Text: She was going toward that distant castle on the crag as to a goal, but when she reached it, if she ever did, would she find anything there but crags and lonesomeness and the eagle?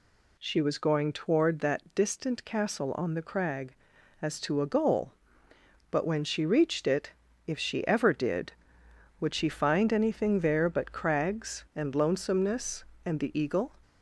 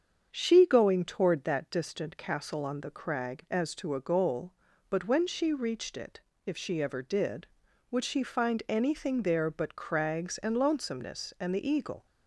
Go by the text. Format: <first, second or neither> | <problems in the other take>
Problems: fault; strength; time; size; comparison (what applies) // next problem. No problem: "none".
first | starts louder than the rest; strong; until 1.3 s; 7.5 dB // skips "was"; at 0.6 s